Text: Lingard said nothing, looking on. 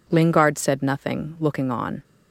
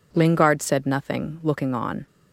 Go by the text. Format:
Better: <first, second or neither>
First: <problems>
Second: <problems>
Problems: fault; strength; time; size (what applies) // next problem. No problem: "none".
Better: neither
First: none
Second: none